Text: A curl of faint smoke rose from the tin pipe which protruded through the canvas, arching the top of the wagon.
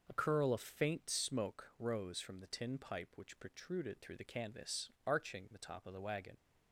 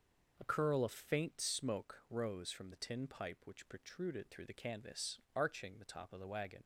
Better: neither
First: none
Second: none

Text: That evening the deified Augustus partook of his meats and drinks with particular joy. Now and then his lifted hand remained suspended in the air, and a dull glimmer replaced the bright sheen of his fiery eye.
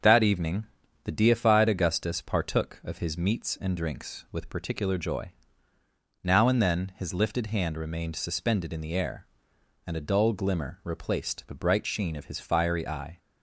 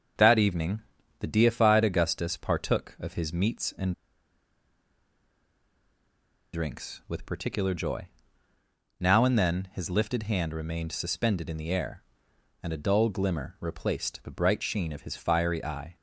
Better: first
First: starts louder than the rest; until 1.4 s; 7 dB // pauses between "evening" and "the"; at 0.6 s; 0.38 s long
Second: starts louder than the rest; until 1.5 s; 7 dB // pauses between "evening" and "the"; at 0.8 s; 0.38 s long // pauses between "and" and "drinks"; strong; at 3.9 s; 2.5 s long

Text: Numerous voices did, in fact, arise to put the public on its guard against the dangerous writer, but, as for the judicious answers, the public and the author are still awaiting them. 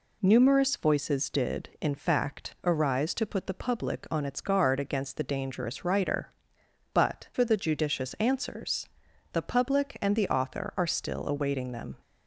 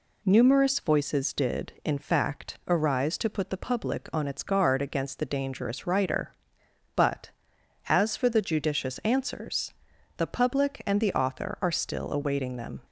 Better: second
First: skips "as"; at 7.3 s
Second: none

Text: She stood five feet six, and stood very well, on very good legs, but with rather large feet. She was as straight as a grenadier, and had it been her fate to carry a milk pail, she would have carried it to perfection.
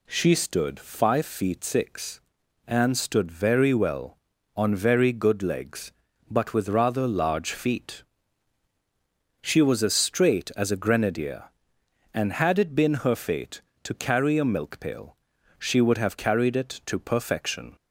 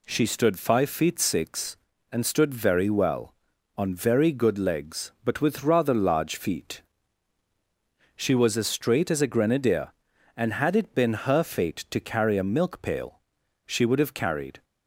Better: first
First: none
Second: stops before "it to perfection"; at 14.6 s

